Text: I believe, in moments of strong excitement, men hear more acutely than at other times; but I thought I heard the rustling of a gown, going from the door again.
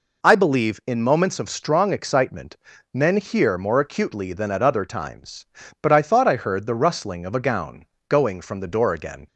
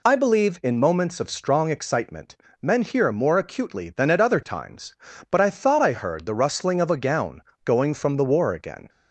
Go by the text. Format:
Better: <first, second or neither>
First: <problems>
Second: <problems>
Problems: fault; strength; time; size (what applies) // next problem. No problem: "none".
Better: first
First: none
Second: says "war" for "door"; at 8.2 s